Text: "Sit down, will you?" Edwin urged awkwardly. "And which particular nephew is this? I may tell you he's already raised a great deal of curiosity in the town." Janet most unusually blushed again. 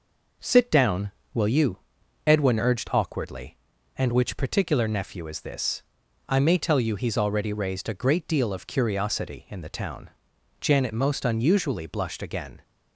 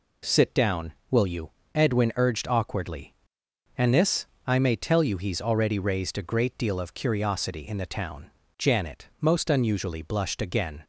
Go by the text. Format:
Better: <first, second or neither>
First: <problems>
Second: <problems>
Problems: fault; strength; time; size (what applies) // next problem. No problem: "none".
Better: first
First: none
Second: skips "which particular nephew is"; at 3.9 s